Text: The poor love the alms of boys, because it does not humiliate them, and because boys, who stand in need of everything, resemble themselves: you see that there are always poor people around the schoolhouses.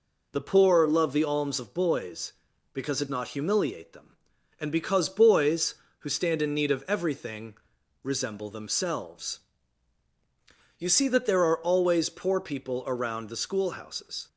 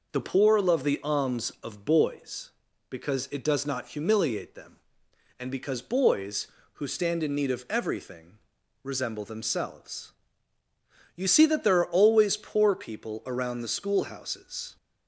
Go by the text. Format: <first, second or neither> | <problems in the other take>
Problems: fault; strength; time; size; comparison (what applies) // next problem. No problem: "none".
second | skips "does"; at 3.0 s